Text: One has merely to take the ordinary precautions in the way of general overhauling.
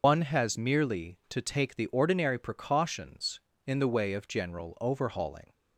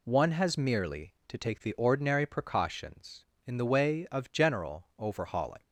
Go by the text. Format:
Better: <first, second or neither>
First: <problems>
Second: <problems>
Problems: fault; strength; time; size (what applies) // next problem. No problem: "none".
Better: second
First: loses the start of "One"; at 0.0 s; 135 ms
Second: none